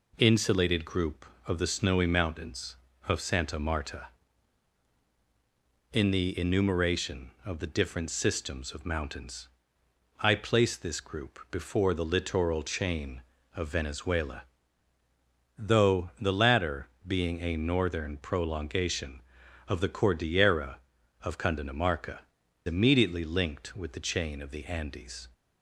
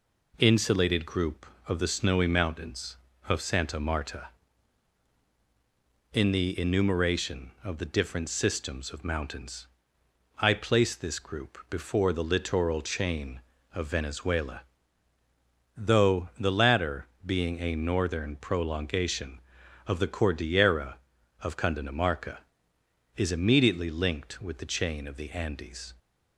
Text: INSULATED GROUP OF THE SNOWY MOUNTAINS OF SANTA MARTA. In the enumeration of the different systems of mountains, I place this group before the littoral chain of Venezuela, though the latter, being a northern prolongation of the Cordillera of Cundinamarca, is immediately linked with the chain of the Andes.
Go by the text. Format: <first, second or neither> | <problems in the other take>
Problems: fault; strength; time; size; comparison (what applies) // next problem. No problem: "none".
second | skips "is"; at 22.4 s